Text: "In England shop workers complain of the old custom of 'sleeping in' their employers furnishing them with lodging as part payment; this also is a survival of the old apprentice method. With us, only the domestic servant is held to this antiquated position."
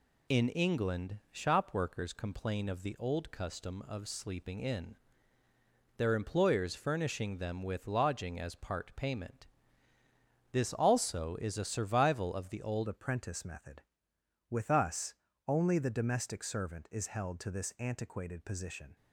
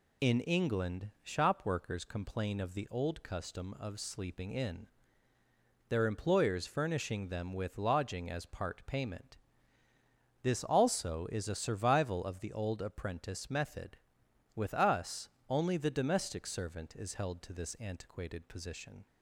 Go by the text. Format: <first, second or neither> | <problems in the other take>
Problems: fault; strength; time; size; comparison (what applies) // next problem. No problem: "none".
second | pauses between "in" and "their"; at 4.9 s; 1.0 s long; also in the second // changes voice at "apprentice"; from 12.8 s on; 6.1 s long